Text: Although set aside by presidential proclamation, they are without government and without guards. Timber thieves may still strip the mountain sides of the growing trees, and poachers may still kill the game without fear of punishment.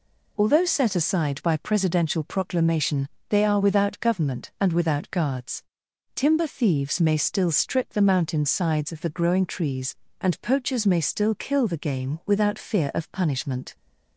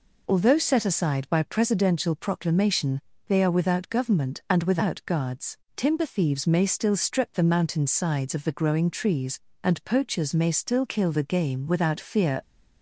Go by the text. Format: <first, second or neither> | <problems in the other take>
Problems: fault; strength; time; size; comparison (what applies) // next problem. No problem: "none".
first | stops before "of punishment"; at 12.4 s